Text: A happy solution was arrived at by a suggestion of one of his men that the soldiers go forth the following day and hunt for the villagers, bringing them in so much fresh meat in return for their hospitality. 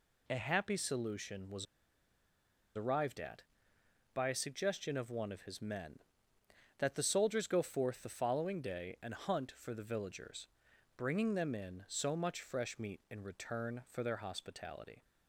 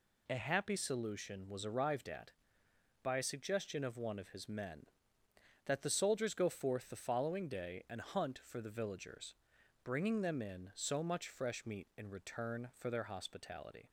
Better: second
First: pauses between "was" and "arrived"; at 1.6 s; 1.1 s long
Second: none

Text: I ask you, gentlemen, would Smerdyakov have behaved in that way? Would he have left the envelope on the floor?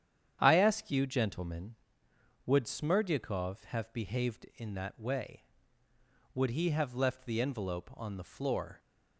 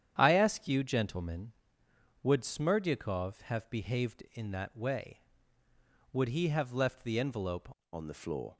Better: first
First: starts louder than the rest; strong; until 1.4 s; 9 dB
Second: starts louder than the rest; strong; until 1.1 s; 9.5 dB // changes voice at "on"; from 7.9 s on; 0.6 s long

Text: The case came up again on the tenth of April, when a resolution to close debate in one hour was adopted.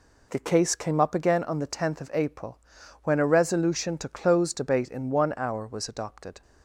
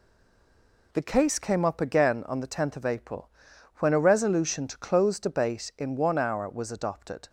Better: first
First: none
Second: stays silent before the first word; slight; until 0.9 s; 0.9 s long

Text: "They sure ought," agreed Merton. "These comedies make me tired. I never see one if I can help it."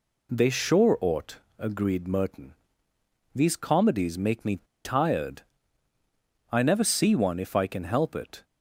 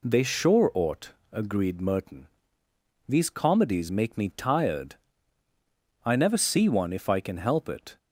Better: second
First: pauses between "me" and "tired"; slight; at 4.6 s; 0.24 s long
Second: none

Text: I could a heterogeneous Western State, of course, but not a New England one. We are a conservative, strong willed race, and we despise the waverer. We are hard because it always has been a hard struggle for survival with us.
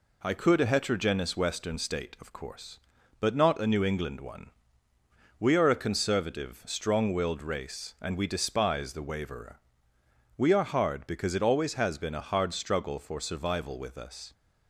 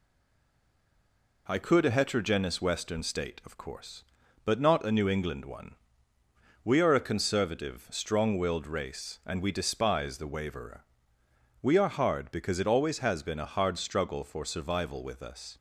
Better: first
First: none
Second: stays silent before the first word; noticeable; until 1.4 s; 1.4 s long

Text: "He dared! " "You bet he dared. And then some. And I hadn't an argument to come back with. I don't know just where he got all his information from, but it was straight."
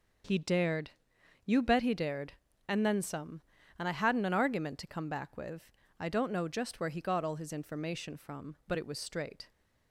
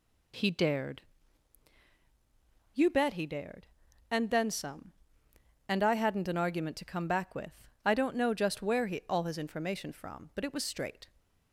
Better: first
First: none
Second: skips "got"; at 9.0 s

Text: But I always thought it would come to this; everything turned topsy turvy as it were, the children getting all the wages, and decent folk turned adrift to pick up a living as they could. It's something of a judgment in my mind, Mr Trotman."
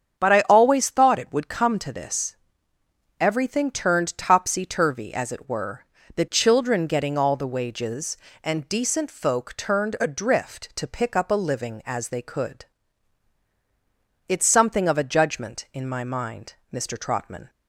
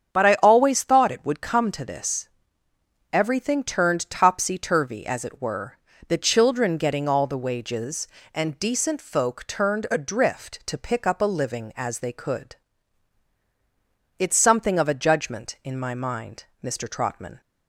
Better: neither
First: starts louder than the rest; strong; until 1.2 s; 7.5 dB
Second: starts louder than the rest; strong; until 1.2 s; 8 dB

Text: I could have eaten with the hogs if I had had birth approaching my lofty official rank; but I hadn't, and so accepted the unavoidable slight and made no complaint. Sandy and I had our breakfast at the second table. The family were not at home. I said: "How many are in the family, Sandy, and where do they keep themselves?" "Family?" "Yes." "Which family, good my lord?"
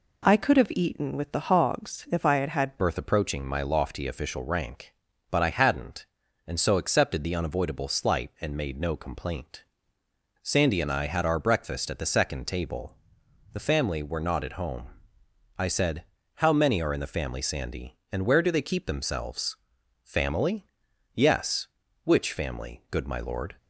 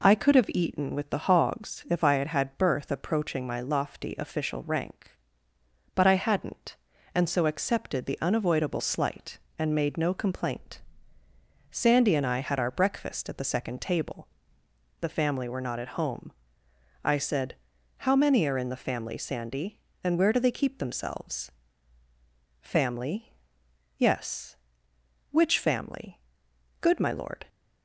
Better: second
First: changes voice at "birth"; from 2.7 s on; 20.8 s long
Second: none

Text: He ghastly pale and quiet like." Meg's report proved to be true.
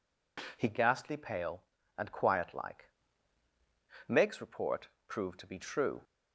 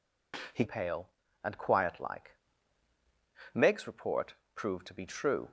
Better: first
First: pauses between "report" and "proved"; slight; at 4.8 s; 0.20 s long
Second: skips "ghastly"; at 0.6 s // pauses between "report" and "proved"; slight; at 4.3 s; 0.22 s long

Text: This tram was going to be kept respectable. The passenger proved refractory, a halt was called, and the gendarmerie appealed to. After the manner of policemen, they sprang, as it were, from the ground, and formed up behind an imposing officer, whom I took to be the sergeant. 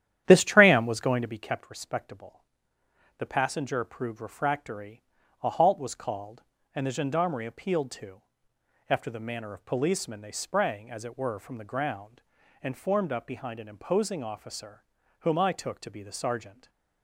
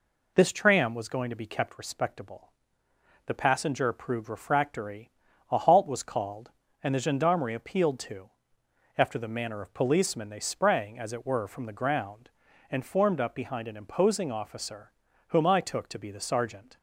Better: second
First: starts louder than the rest; strong; until 1.4 s; 11 dB // stays silent after the last word; slight; from 16.4 s on; 0.6 s long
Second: none

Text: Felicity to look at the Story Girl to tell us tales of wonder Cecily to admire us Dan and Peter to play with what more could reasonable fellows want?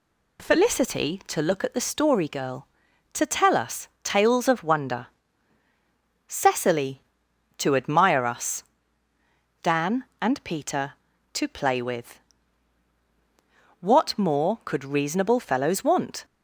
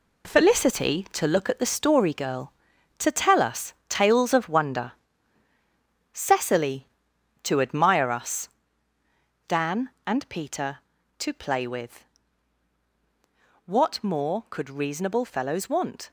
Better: first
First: pauses between "wonder" and "Cecily"; at 5.0 s; 1.2 s long // pauses between "us" and "Dan"; noticeable; at 8.6 s; 0.98 s long // pauses between "with" and "what"; strong; at 12.1 s; 1.6 s long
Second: gets quieter; strong; throughout; 7.5 dB // pauses between "wonder" and "Cecily"; at 4.9 s; 1.2 s long // pauses between "us" and "Dan"; noticeable; at 8.4 s; 0.98 s long // pauses between "with" and "what"; strong; at 12.0 s; 1.6 s long

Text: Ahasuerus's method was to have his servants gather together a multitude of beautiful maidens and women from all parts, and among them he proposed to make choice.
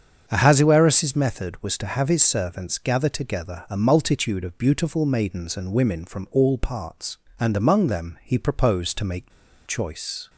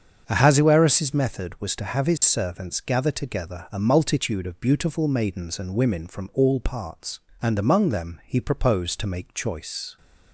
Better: second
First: starts louder than the rest; until 1.2 s; 7 dB // pauses between "make" and "choice"; slight; at 9.3 s; 0.35 s long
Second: starts louder than the rest; until 1.2 s; 7 dB

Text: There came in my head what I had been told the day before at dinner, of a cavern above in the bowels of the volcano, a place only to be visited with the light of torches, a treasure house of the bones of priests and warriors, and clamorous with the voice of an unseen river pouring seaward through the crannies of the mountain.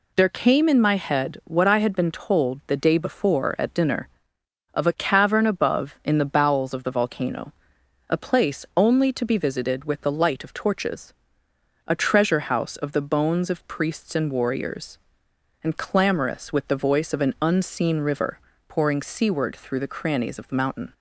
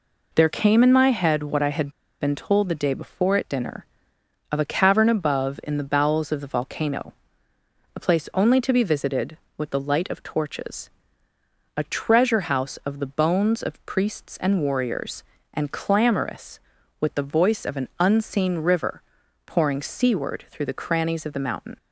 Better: first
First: pauses between "river" and "pouring"; slight; at 18.3 s; 0.30 s long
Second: pauses between "had" and "been"; slight; at 1.8 s; 0.31 s long // pauses between "river" and "pouring"; noticeable; at 19.0 s; 0.46 s long

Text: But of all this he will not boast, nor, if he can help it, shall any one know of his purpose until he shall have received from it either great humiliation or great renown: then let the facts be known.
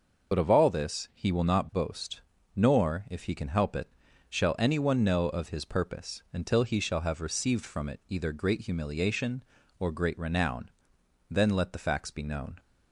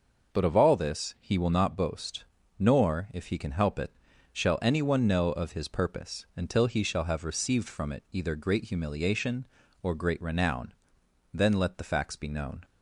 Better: second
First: loses the start of "But"; at 0.3 s; 50 ms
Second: none

